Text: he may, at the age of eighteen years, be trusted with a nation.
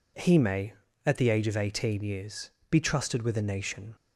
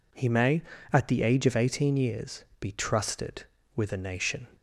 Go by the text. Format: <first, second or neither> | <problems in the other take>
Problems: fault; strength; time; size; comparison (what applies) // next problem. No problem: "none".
neither | none